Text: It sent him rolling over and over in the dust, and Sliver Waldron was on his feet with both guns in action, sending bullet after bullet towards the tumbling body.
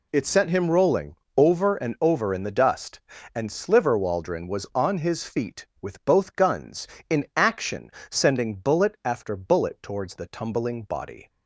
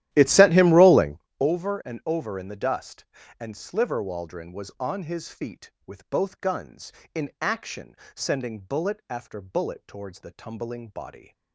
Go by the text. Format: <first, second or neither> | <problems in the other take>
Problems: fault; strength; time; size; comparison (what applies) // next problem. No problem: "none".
first | starts louder than the rest; strong; until 1.3 s; 13 dB // pauses between "rolling" and "over"; slight; at 1.1 s; 0.20 s long; slight in the first